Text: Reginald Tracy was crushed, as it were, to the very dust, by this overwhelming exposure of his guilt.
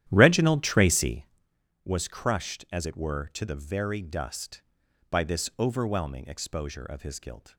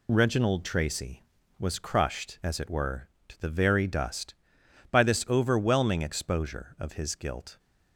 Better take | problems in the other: second | starts louder than the rest; strong; until 1.4 s; 11.5 dB

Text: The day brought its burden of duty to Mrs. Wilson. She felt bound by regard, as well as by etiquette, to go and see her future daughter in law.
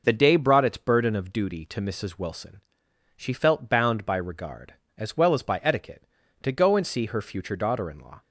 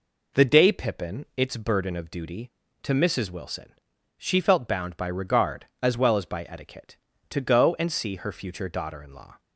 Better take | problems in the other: first | says "pippin" for "brought"; at 0.7 s

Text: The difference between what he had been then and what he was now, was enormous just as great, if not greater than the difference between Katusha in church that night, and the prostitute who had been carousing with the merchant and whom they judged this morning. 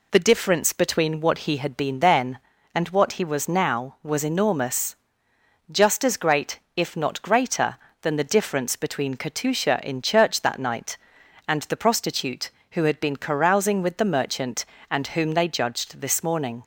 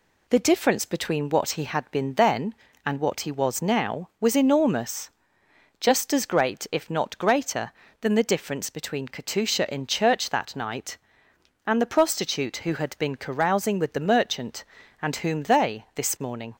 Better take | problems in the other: first | pauses between "enormous" and "just"; noticeable; at 5.1 s; 0.68 s long; noticeable in the first // skips "judged"; at 15.8 s

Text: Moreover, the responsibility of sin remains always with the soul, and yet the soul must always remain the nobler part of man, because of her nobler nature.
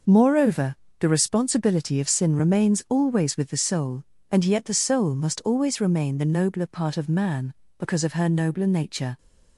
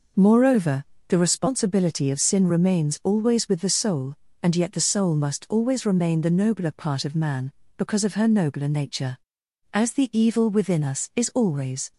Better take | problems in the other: first | goes on to say "As the evil within us is always"; strong; from 9.7 s on; 2.2 s long

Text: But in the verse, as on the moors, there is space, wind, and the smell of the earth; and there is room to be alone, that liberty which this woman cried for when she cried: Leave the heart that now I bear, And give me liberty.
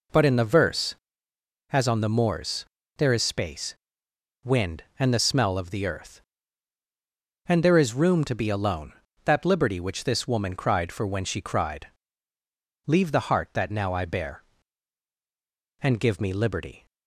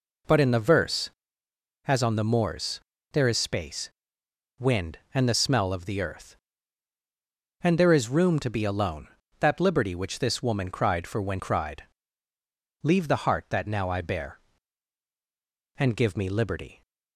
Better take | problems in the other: first | skips "she"; at 11.3 s

